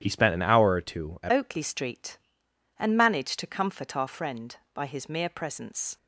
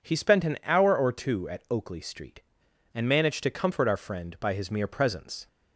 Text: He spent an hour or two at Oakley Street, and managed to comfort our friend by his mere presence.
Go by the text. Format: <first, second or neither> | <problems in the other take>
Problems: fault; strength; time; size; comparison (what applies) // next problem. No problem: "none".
second | starts louder than the rest; strong; until 1.0 s; 10.5 dB // changes voice at "Oakley"; from 1.3 s on; 4.6 s long